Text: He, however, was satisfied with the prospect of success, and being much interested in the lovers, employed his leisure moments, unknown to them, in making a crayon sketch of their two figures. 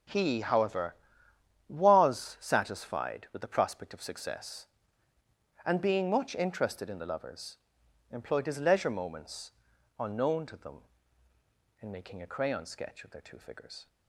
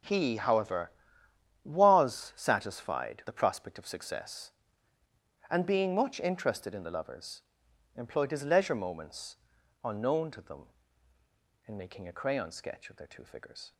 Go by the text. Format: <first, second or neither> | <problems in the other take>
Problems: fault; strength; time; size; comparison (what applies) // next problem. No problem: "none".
first | skips "with"; at 3.2 s